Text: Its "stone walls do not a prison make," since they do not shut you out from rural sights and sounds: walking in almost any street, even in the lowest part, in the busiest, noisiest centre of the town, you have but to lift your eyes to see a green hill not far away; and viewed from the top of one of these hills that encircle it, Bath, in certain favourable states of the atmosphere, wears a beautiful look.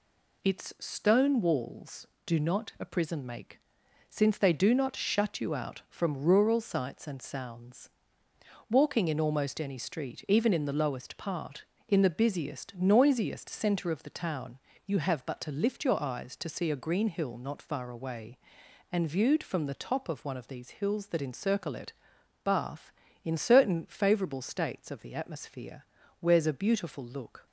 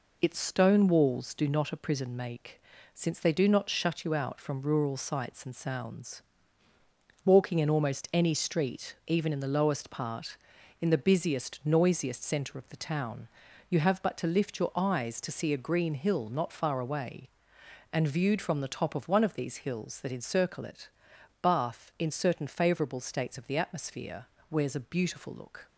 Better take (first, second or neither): neither